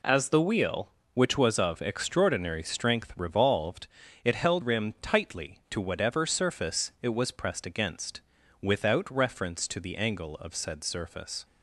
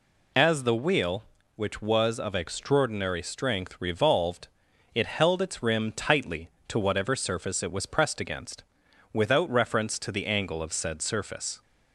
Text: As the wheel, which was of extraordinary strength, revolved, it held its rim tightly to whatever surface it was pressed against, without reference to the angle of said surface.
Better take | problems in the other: second | skips "its"; at 4.6 s

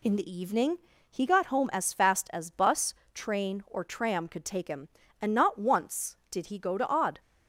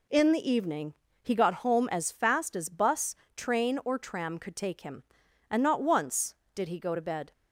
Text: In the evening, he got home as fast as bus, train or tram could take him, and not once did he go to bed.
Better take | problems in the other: second | says "odd" for "bed"; at 6.8 s

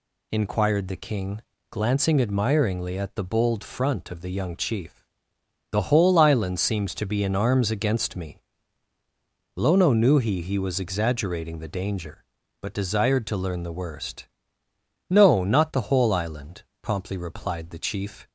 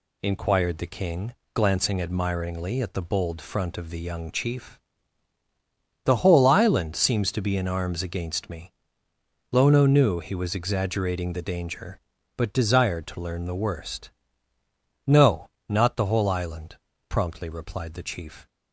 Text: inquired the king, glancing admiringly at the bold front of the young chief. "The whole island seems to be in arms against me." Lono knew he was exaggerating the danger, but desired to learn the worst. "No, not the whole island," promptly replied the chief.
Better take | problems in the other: second | says "he" twice; at 10.4 s

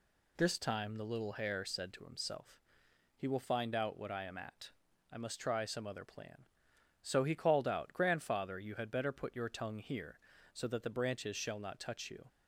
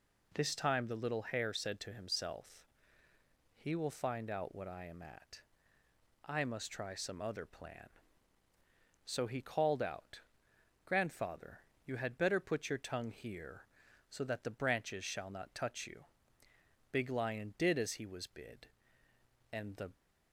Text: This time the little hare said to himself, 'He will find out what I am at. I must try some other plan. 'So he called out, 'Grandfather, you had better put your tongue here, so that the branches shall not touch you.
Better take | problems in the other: first | goes on to say "Big Lion did as he was bid and the"; strong; from 16.9 s on; 3.0 s long

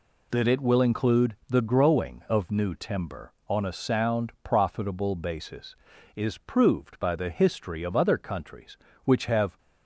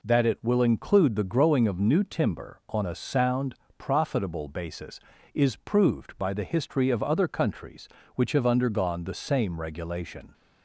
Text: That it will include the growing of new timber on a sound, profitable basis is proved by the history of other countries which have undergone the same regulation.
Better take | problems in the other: second | stops before "undergone the same regulation"; at 9.5 s

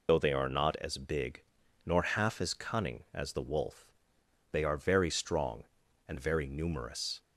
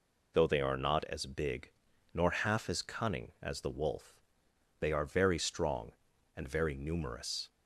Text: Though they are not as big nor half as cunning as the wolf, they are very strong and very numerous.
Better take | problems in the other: second | loses the start of "Though"; at 0.0 s; 35 ms // pauses between "big" and "nor"; at 1.4 s; 0.42 s long; also in the second

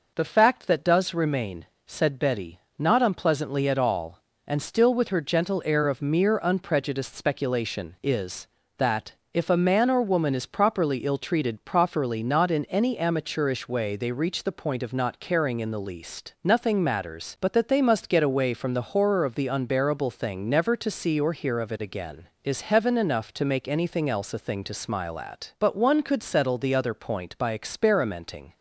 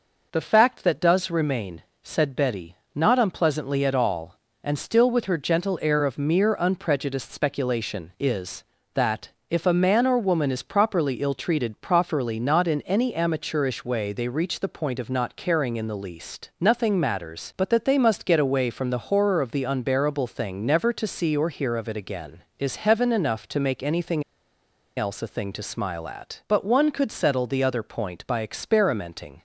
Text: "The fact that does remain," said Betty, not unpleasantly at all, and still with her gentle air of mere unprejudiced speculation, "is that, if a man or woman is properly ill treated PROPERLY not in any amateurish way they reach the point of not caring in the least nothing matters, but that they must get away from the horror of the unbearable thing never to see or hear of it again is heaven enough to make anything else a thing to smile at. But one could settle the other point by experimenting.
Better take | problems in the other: first | pauses between "anything" and "else"; noticeable; at 24.2 s; 0.74 s long

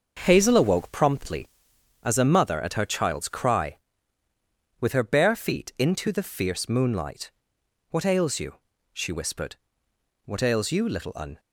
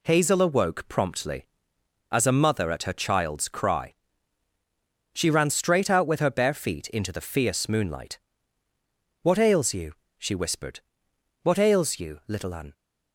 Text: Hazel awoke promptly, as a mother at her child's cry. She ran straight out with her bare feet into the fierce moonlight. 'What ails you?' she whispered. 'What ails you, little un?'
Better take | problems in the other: second | starts louder than the rest; until 1.2 s; 6 dB // skips "She ran straight out"; at 4.2 s

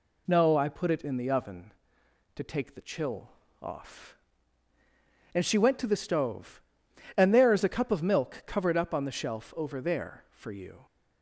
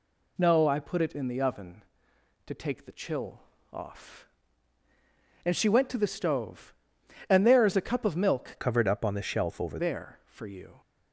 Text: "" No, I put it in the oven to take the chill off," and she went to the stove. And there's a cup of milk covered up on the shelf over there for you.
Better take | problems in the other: first | pauses between "chill" and "off"; slight; at 3.4 s; 0.32 s long; slight in the first // changes voice from "covered" to "over"; from 8.5 to 9.7 s; 1.2 s long

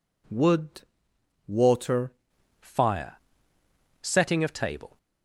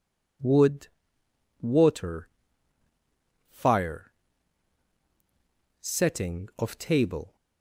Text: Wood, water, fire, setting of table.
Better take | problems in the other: second | changes voice at "fire"; from 2.6 s on; 2.3 s long

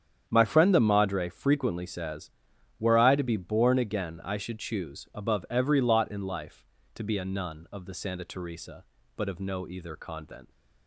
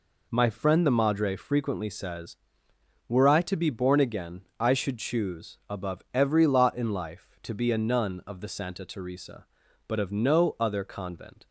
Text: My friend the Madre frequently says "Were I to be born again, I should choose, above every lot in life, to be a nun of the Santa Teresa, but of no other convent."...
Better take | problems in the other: second | starts louder than the rest; strong; until 1.2 s; 8.5 dB // says "either" for "other"; at 9.6 s

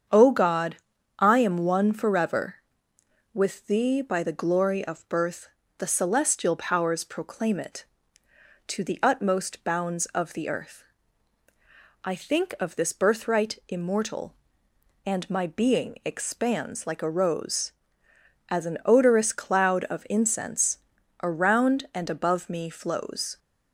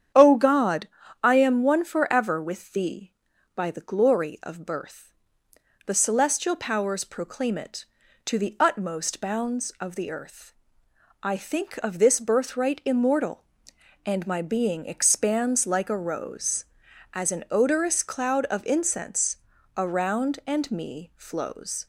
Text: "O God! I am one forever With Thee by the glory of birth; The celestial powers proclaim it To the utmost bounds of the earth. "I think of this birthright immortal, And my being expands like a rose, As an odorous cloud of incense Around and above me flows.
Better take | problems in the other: first | starts louder than the rest; strong; until 1.4 s; 9 dB; strong in the first // pauses between "incense" and "Around"; at 19.3 s; 0.40 s long; also in the first // skips "above"; at 20.7 s

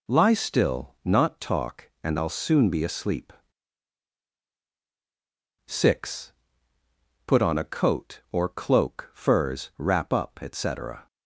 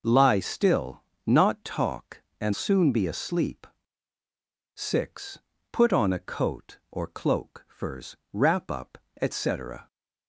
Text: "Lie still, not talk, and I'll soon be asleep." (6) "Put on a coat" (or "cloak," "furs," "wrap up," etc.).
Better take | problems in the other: first | skips "I'll"; at 2.5 s

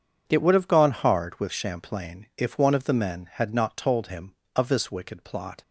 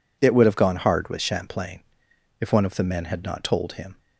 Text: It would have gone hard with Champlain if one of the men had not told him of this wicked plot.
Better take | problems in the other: first | pauses between "Champlain" and "if"; noticeable; at 1.8 s; 0.60 s long // stops before "of this wicked plot"; at 3.9 s

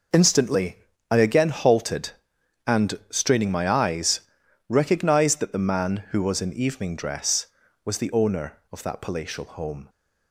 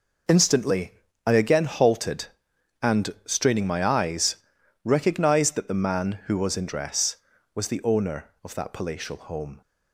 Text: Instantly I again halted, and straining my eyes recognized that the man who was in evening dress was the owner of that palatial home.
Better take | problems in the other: first | pauses between "Instantly" and "I"; slight; at 0.9 s; 0.34 s long; slight in the first // pauses between "eyes" and "recognized"; noticeable; at 4.3 s; 0.48 s long; noticeable in the first // skips "evening"; at 6.6 s

